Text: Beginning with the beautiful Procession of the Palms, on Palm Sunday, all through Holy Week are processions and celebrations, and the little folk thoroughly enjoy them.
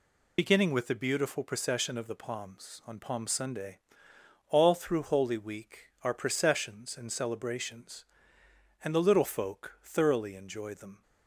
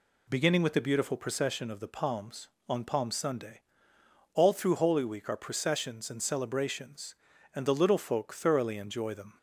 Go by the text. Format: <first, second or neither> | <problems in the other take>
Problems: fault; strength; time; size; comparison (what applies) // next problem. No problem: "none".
second | loses the start of "Beginning"; at 0.3 s; 50 ms